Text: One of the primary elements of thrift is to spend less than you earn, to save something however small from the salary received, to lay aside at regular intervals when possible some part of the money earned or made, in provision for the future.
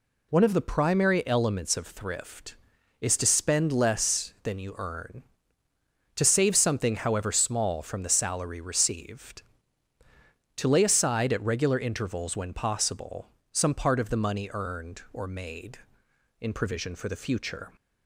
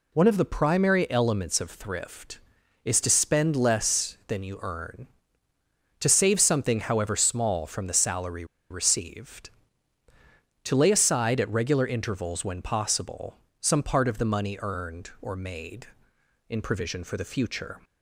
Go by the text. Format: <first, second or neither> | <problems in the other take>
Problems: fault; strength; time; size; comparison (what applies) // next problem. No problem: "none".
first | pauses between "salary" and "received"; slight; at 8.4 s; 0.26 s long // pauses between "possible" and "some"; slight; at 13.3 s; 0.24 s long; slight in the first